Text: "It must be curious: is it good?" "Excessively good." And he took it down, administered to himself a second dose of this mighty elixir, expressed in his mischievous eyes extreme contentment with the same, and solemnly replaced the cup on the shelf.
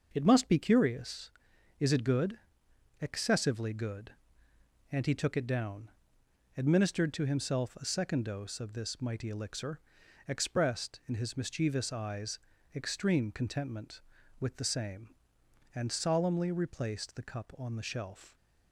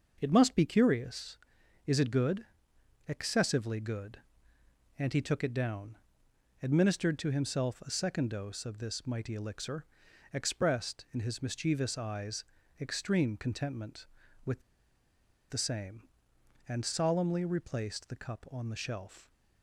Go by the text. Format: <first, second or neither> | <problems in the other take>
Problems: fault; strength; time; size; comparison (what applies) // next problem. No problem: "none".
first | starts louder than the rest; noticeable; until 1.2 s; 6 dB; noticeable in the first // pauses between "eyes" and "extreme"; at 12.4 s; 0.38 s long; also in the first // pauses between "with" and "the"; noticeable; at 14.6 s; 0.89 s long